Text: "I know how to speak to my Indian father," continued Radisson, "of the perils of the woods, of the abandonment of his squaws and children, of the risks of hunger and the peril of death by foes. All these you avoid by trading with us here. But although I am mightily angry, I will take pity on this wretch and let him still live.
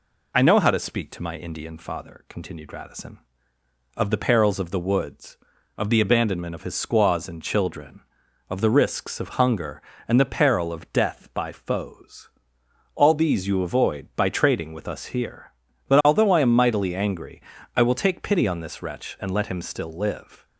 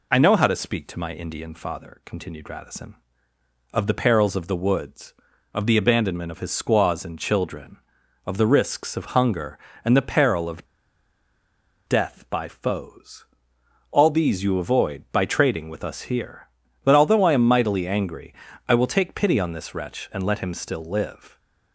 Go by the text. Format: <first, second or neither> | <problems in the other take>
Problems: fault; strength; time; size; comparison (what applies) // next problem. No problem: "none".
first | pauses between "of" and "death"; at 10.6 s; 1.2 s long